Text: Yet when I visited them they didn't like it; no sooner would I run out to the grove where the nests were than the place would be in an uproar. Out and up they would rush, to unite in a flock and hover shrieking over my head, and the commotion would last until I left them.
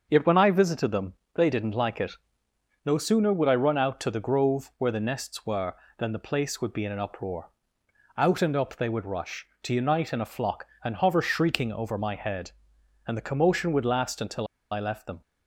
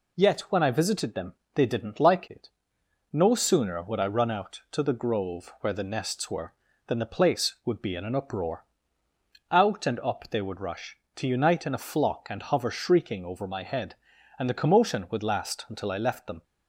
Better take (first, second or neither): second